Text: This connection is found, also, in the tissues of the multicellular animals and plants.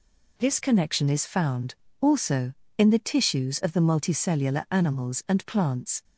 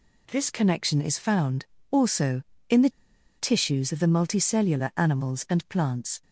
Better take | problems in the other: first | pauses between "the" and "tissues"; noticeable; at 2.8 s; 0.48 s long

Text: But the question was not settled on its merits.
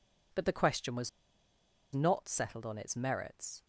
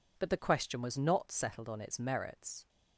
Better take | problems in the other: second | pauses between "was" and "not"; noticeable; at 1.0 s; 0.85 s long

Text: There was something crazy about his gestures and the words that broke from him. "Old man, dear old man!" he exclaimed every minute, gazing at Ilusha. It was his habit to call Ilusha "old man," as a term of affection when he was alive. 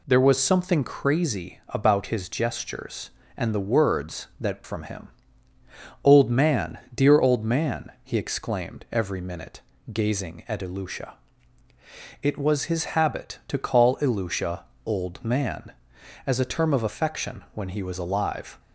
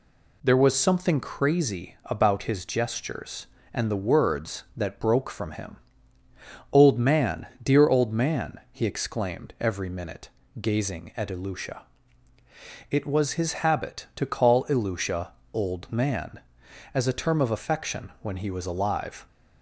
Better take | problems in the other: second | skips "broke"; at 4.6 s // pauses between "Ilusha" and "old"; slight; at 14.6 s; 0.20 s long; slight in the second

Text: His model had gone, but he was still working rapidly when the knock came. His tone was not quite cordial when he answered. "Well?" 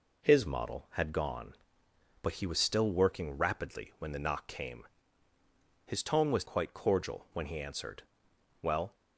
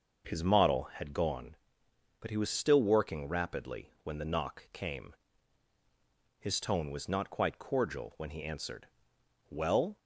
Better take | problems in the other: second | skips "not"; at 6.4 s

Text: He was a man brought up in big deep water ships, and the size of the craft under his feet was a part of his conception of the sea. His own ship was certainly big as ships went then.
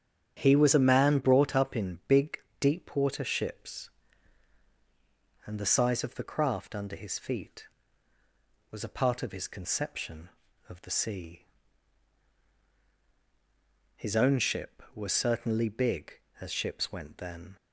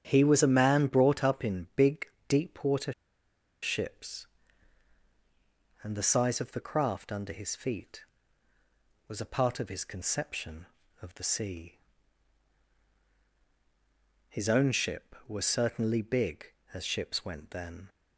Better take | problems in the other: first | starts louder than the rest; strong; until 1.0 s; 9 dB; strong in the first // pauses between "big" and "deep"; slight; at 2.0 s; 0.22 s long; slight in the first // pauses between "water" and "ships"; noticeable; at 2.9 s; 0.70 s long

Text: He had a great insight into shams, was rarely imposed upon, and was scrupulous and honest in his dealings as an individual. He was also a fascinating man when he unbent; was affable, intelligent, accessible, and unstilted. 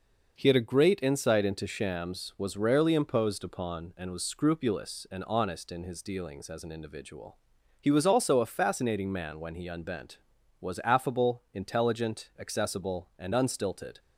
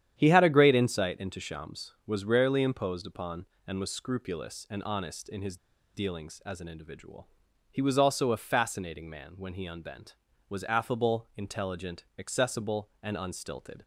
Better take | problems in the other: first | starts louder than the rest; strong; until 1.1 s; 10 dB // pauses between "his" and "dealings"; at 5.5 s; 0.38 s long

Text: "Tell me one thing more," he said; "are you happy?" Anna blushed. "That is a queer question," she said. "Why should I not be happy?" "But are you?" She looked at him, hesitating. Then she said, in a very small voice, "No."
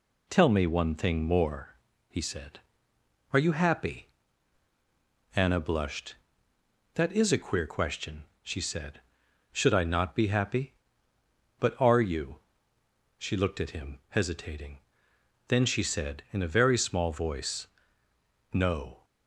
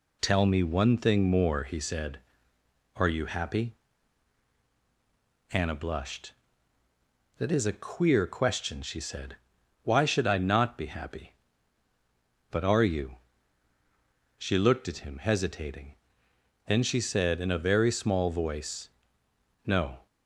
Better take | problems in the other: second | skips "Why"; at 9.2 s

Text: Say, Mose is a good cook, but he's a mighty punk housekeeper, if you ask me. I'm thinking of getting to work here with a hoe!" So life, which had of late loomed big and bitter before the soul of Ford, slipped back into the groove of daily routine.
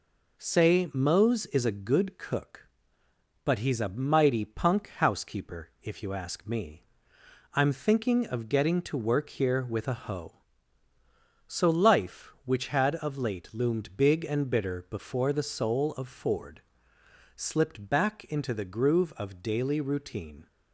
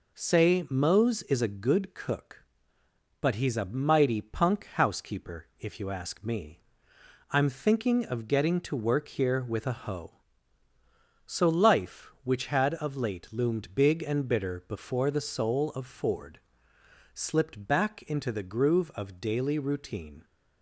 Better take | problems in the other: neither | none

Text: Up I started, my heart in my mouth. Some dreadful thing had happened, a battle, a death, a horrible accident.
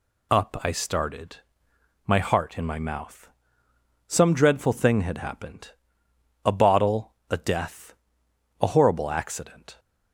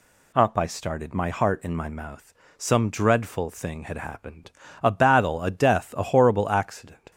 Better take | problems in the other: second | says "bottle" for "battle"; at 6.5 s

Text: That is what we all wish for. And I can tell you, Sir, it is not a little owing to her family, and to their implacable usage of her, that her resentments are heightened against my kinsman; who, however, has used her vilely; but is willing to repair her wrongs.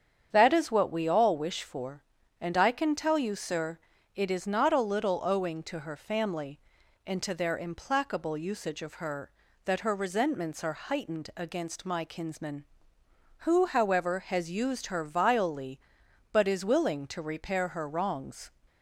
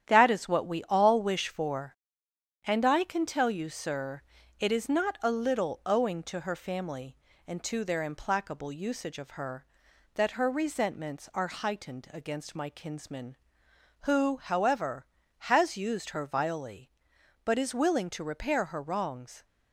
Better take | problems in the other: first | gets quieter; throughout; 6 dB // starts louder than the rest; strong; until 1.1 s; 10 dB; strong in the first

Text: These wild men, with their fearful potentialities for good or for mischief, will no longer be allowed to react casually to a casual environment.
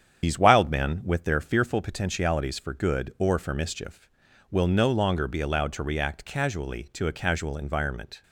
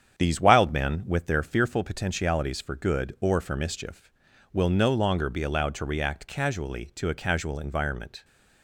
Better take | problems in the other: second | loses the start of "These"; at 0.2 s; 65 ms // starts louder than the rest; strong; until 1.2 s; 8.5 dB; strong in the second

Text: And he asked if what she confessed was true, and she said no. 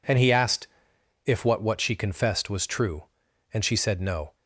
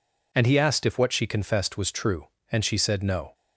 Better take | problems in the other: second | pauses between "asked" and "if"; noticeable; at 0.6 s; 0.58 s long // says "what" twice; at 1.6 s

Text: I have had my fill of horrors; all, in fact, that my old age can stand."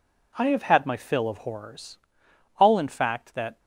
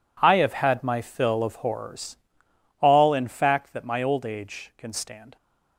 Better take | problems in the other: second | stops before "my old age can stand"; at 3.5 s

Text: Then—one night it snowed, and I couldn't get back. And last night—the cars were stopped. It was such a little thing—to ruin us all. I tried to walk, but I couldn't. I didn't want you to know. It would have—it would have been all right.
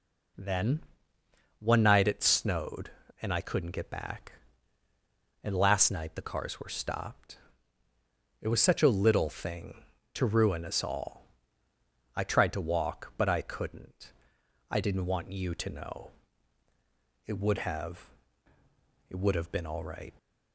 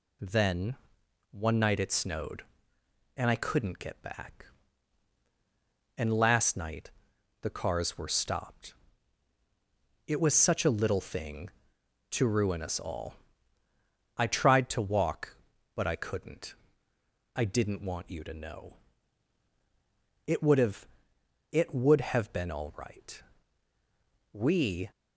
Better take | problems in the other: first | goes on to say "We"; from 24.3 s on; 0.56 s long

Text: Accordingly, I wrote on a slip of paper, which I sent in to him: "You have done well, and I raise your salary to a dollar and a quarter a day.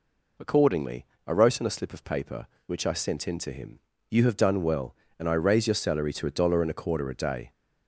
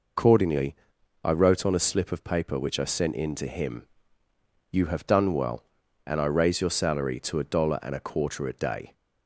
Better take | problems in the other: first | loses the start of "Accordingly"; at 0.1 s; 105 ms

